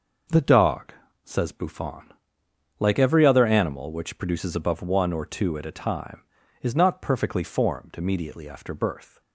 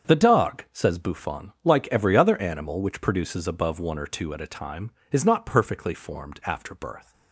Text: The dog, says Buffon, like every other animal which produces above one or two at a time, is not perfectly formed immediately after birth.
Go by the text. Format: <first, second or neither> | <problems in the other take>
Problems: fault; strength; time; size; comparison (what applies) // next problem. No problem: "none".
first | starts louder than the rest; strong; until 1.1 s; 7 dB // skips "immediately"; at 6.4 s